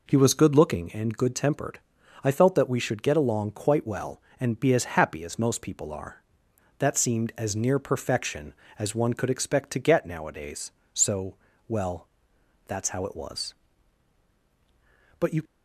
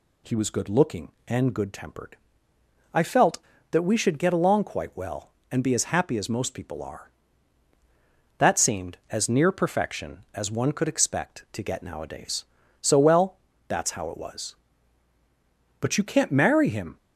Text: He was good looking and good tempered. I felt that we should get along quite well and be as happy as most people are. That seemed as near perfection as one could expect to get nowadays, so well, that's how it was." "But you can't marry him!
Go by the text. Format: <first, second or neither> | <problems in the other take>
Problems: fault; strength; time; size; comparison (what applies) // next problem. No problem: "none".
second | pauses between "so" and "well"; slight; at 11.3 s; 0.32 s long // stops before "can't marry him"; at 15.4 s